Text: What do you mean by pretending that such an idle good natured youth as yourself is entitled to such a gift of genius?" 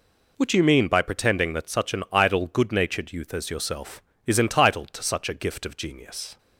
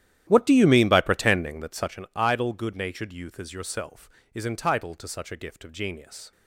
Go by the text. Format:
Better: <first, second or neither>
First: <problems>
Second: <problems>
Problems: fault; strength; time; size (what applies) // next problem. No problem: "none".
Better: first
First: none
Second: starts louder than the rest; strong; until 2.0 s; 12 dB